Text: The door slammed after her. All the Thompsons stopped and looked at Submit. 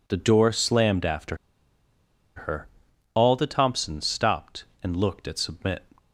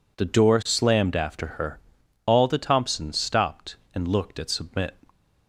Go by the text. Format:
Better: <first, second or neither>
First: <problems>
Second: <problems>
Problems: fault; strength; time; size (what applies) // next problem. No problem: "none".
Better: second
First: pauses between "after" and "her"; at 1.3 s; 1.0 s long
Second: none